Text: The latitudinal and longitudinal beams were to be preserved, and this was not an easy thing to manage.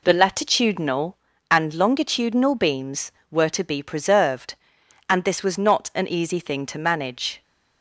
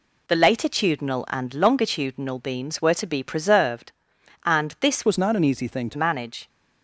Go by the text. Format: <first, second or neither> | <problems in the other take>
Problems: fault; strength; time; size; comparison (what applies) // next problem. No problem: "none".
first | changes voice from "was" to "to"; from 5.0 to 5.9 s; 0.9 s long